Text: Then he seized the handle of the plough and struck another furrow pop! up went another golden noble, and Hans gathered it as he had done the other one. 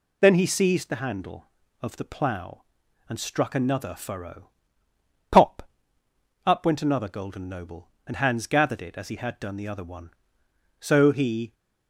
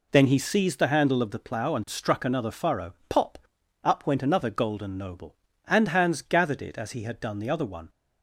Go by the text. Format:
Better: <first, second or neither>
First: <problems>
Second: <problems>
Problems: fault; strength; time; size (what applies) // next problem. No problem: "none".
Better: second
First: pauses between "furrow" and "pop"; noticeable; at 4.4 s; 0.80 s long // goes on to say "So he"; noticeable; from 10.7 s on; 0.76 s long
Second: pauses between "furrow" and "pop"; slight; at 2.9 s; 0.16 s long